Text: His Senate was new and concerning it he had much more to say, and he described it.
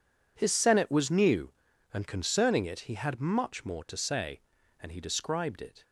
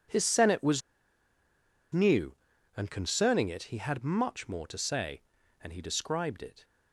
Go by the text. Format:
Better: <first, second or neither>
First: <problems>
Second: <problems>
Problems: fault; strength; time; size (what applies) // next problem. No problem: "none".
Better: first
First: none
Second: pauses between "was" and "new"; at 0.8 s; 1.1 s long